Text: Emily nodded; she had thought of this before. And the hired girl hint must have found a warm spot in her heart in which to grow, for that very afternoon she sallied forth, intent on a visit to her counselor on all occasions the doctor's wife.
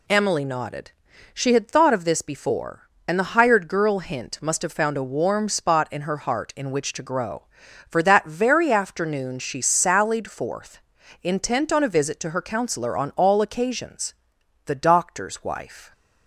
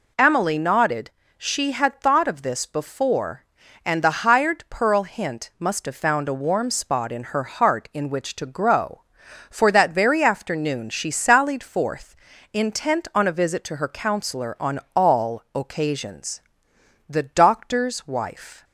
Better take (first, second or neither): first